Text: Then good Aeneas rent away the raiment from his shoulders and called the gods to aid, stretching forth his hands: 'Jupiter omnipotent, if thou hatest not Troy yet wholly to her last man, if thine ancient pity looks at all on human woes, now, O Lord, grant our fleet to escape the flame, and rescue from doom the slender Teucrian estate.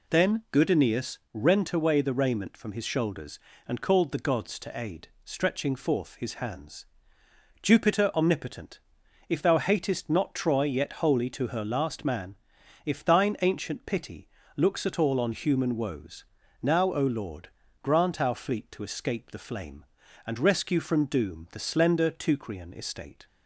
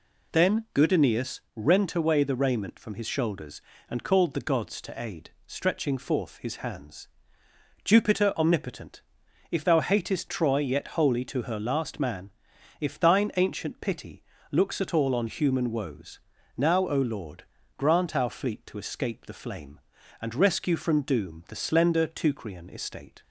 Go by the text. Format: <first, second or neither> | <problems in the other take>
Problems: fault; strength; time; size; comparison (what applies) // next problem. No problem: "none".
first | pauses between "Aeneas" and "rent"; slight; at 1.3 s; 0.16 s long; slight in the first // skips "not"; at 10.2 s // pauses between "pity" and "looks"; slight; at 14.2 s; 0.26 s long; slight in the first